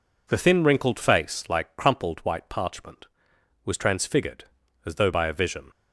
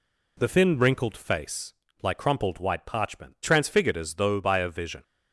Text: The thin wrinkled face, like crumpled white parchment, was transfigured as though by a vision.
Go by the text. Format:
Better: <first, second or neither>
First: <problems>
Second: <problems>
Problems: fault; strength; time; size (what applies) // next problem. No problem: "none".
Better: first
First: none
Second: skips "was"; at 3.3 s